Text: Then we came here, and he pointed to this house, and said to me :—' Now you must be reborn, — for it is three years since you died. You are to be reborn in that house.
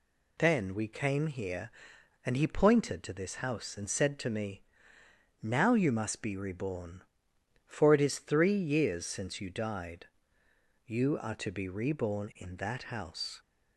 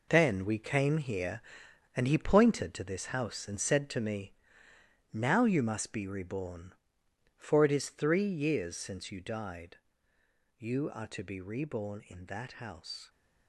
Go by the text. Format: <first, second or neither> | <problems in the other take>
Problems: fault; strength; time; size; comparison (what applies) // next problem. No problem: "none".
first | gets quieter; strong; throughout; 8.5 dB